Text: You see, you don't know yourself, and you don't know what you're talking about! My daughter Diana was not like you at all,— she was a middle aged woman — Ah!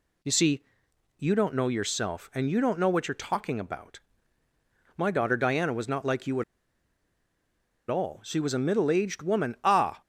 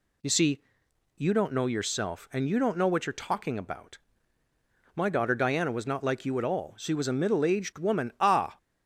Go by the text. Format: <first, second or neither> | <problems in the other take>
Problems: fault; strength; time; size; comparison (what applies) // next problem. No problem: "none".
second | pauses between "at" and "all"; strong; at 6.4 s; 1.4 s long